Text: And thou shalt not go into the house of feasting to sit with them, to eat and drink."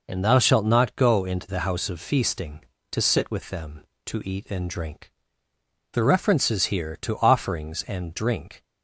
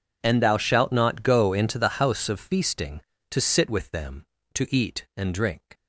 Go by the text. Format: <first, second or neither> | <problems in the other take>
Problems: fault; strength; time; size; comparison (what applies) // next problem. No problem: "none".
second | goes on to say "The references here to offerings and drink"; strong; from 5.9 s on; 2.7 s long